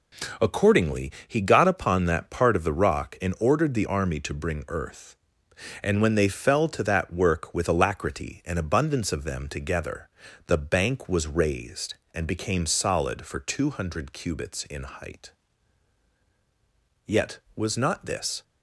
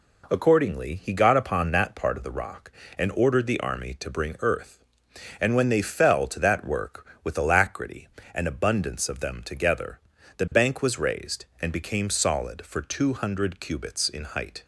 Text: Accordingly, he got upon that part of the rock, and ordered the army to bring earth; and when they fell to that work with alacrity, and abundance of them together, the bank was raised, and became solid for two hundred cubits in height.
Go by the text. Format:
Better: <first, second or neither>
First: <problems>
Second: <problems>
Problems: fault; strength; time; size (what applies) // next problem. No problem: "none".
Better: second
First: goes on to say "Yet was not this"; from 17.0 s on; 1.3 s long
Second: none